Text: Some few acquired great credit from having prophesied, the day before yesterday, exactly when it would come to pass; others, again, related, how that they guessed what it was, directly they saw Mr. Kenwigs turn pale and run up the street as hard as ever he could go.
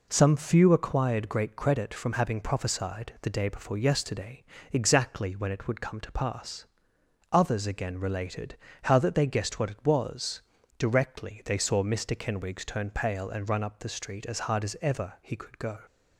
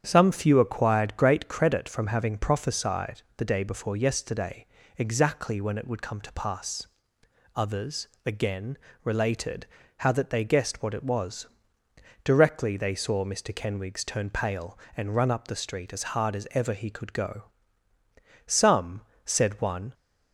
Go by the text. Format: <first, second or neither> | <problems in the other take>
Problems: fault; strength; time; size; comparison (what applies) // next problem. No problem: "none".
first | starts louder than the rest; strong; until 1.0 s; 8.5 dB // goes on to say "Some said one"; from 18.4 s on; 1.4 s long